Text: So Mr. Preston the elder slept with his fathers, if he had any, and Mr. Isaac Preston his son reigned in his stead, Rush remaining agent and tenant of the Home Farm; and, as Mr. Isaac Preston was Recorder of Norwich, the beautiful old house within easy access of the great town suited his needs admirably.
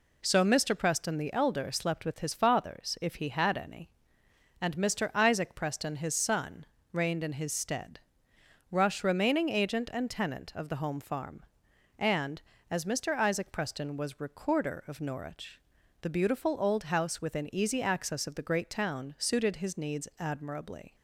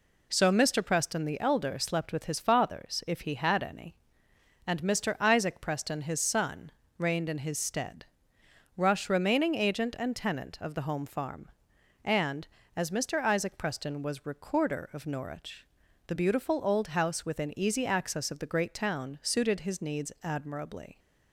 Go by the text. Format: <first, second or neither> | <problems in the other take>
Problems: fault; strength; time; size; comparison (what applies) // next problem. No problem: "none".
neither | pauses between "son" and "reigned"; slight; the same in both